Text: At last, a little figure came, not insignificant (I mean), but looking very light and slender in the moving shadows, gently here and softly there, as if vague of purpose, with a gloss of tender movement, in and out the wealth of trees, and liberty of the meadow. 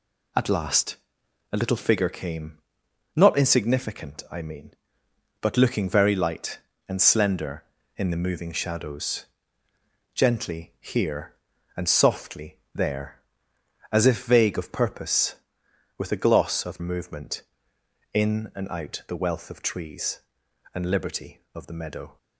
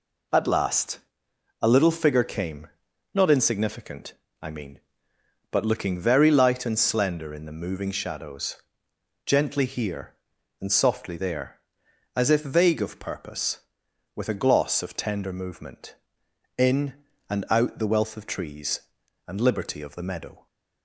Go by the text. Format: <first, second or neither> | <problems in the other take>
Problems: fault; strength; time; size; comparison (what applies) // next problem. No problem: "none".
second | pauses between "softly" and "there"; slight; at 12.5 s; 0.16 s long // skips "tender"; at 16.7 s